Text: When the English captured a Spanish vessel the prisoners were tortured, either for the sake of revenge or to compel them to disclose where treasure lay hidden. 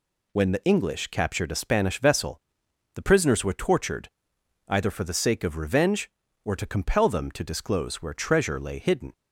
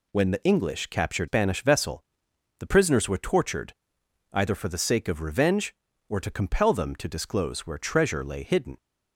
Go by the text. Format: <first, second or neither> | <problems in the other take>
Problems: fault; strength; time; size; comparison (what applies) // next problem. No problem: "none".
first | skips "a"; at 1.2 s // pauses between "vessel" and "the"; noticeable; at 2.0 s; 0.58 s long; noticeable in the first